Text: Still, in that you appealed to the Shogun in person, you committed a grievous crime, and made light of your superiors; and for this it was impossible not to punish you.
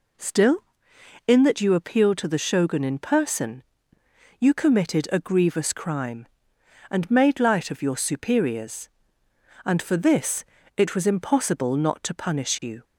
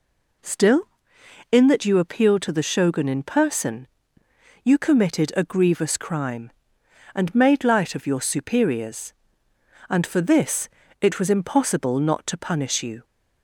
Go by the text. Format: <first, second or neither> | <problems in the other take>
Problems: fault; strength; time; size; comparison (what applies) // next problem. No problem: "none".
neither | pauses between "this" and "it"; slight; the same in both